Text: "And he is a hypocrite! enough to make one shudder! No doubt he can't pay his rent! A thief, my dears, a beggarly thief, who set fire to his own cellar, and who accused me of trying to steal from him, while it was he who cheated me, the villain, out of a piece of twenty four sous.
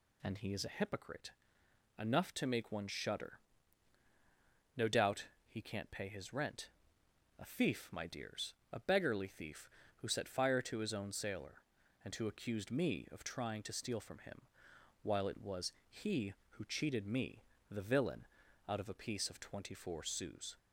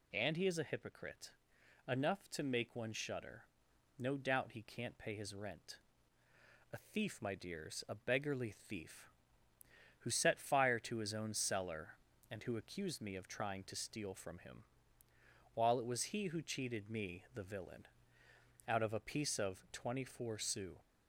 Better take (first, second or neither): second